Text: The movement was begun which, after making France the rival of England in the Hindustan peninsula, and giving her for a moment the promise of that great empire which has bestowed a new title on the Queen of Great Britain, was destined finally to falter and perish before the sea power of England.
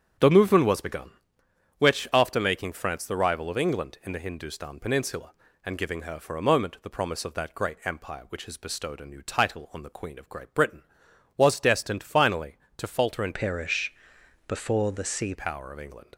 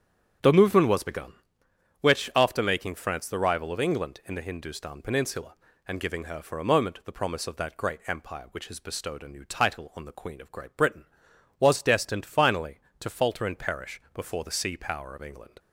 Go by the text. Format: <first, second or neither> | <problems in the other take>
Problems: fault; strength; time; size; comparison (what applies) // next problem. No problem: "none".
second | starts louder than the rest; strong; until 1.9 s; 8.5 dB; strong in the second // changes voice from "perish" to "sea"; from 13.3 to 15.3 s; 2.0 s long // pauses between "perish" and "before"; noticeable; at 13.9 s; 0.56 s long